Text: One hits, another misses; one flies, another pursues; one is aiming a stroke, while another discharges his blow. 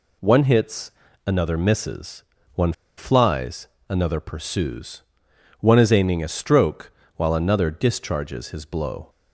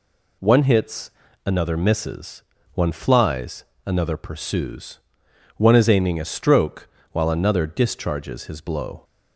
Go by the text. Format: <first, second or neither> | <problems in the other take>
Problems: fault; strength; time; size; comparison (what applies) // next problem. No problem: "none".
second | pauses between "one" and "flies"; slight; at 2.7 s; 0.24 s long